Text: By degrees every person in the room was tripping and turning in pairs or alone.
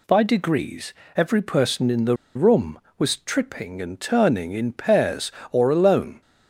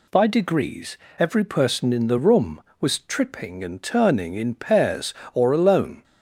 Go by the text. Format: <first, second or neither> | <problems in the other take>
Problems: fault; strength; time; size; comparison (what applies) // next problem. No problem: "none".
second | pauses between "degrees" and "every"; slight; at 0.9 s; 0.24 s long; slight in the second // pauses between "the" and "room"; slight; at 2.1 s; 0.20 s long